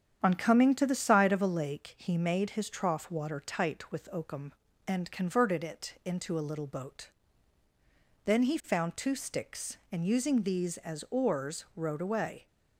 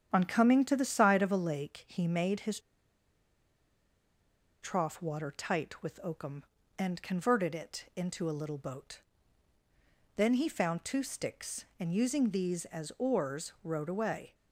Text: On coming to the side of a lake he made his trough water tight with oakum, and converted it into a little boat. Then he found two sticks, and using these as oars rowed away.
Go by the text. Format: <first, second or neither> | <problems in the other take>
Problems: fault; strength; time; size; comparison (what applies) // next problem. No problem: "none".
first | starts louder than the rest; strong; until 1.1 s; 9 dB; strong in the first // pauses between "his" and "trough"; strong; at 2.5 s; 2.0 s long